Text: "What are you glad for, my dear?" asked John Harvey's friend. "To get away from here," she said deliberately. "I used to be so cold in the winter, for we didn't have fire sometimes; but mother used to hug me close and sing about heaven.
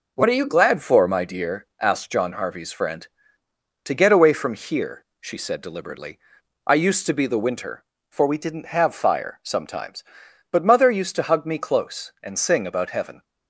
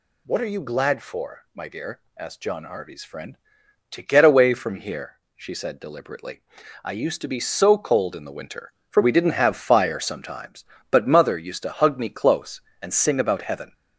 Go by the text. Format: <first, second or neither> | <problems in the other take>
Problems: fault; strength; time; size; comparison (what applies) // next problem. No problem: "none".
second | skips "so cold in"; at 7.2 s